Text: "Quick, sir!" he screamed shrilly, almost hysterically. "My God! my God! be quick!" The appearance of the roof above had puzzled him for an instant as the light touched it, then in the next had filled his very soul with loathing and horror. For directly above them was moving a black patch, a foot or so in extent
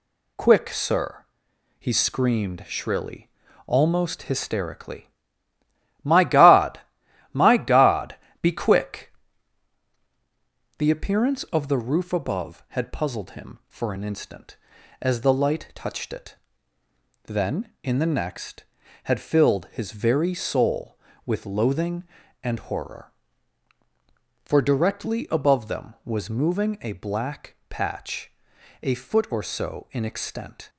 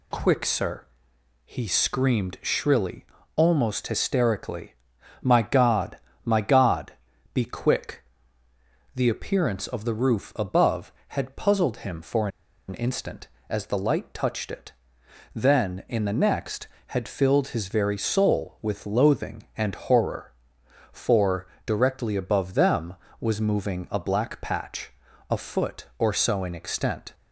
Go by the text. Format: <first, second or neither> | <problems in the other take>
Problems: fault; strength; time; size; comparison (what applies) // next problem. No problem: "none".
first | pauses between "for" and "an"; at 12.2 s; 0.40 s long // pauses between "For" and "directly"; slight; at 21.4 s; 0.18 s long